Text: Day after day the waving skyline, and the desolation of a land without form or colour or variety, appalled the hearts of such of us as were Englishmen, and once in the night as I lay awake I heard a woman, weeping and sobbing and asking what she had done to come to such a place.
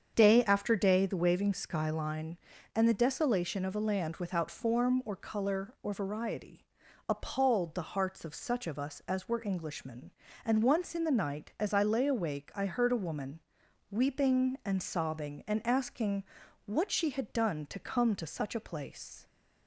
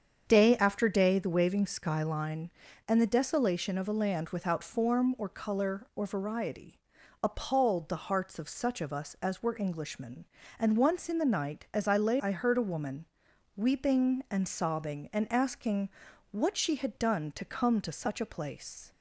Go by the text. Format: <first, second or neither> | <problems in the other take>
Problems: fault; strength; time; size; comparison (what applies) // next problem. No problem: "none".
first | starts louder than the rest; strong; until 1.2 s; 7.5 dB; strong in the first // skips "awake"; at 12.1 s // pauses between "asking" and "what"; at 15.8 s; 0.44 s long; also in the first